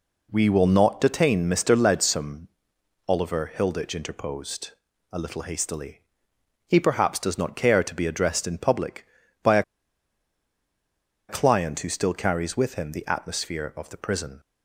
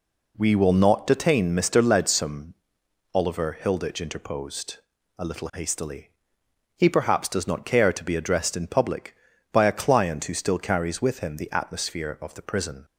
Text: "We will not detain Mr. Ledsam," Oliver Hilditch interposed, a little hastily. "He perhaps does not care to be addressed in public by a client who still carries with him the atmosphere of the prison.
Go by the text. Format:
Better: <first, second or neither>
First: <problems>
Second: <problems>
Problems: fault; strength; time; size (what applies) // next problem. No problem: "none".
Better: second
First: pauses between "a" and "client"; strong; at 9.6 s; 1.6 s long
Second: none